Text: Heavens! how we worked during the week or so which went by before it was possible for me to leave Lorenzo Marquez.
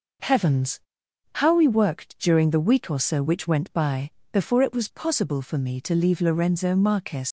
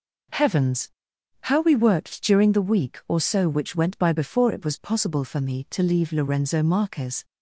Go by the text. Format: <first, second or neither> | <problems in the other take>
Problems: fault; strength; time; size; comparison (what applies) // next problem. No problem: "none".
second | pauses between "by" and "before"; slight; at 4.1 s; 0.22 s long // leaves "Marquez" unfinished; at 7.2 s; 105 ms